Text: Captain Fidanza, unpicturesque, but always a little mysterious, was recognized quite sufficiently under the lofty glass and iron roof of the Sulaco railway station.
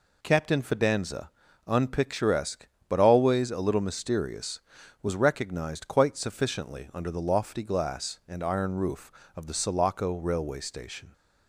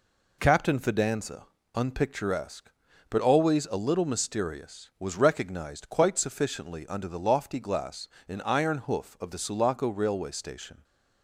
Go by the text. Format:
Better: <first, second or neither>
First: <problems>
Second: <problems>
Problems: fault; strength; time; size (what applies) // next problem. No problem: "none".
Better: first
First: none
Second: says "hoof" for "roof"; at 8.7 s